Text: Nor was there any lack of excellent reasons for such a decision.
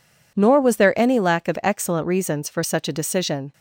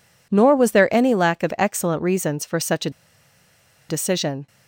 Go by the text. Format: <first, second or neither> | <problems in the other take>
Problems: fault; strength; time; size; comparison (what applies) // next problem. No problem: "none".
first | pauses between "a" and "decision"; at 2.8 s; 0.99 s long